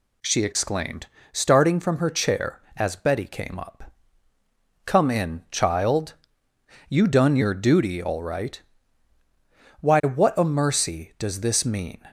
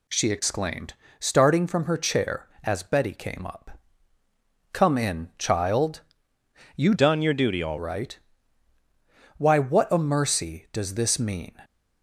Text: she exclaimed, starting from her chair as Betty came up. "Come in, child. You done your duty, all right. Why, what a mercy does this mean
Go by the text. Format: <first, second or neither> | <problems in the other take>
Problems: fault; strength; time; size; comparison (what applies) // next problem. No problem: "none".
first | changes voice from "done" to "all"; from 6.9 to 7.7 s; 0.8 s long